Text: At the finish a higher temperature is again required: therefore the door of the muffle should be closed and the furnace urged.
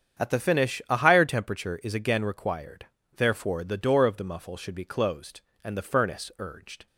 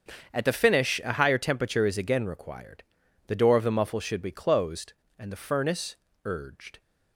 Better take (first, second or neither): first